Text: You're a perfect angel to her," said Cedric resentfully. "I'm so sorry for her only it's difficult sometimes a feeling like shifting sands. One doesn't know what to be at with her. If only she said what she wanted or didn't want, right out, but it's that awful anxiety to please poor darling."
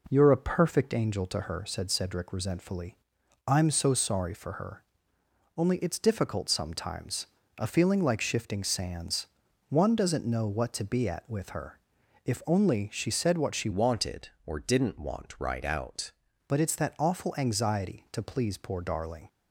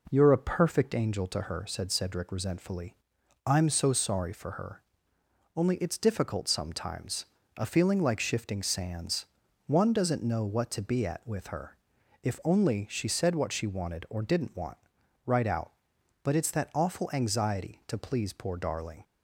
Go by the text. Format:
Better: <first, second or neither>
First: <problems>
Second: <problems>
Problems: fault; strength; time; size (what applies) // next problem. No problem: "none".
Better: second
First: pauses between "her" and "only"; noticeable; at 4.8 s; 0.74 s long // pauses between "sometimes" and "a"; slight; at 7.2 s; 0.32 s long // changes voice from "wanted" to "out"; from 13.7 to 16.1 s; 2.4 s long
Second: pauses between "her" and "only"; noticeable; at 4.8 s; 0.74 s long // pauses between "sometimes" and "a"; slight; at 7.2 s; 0.32 s long